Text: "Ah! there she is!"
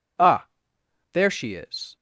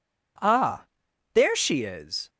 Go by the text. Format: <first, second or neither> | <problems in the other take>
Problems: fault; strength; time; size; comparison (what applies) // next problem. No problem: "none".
neither | none